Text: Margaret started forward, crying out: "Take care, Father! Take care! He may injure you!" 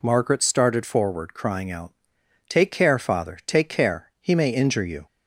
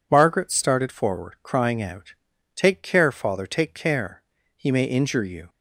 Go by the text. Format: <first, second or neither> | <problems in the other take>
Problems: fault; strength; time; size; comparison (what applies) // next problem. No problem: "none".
neither | none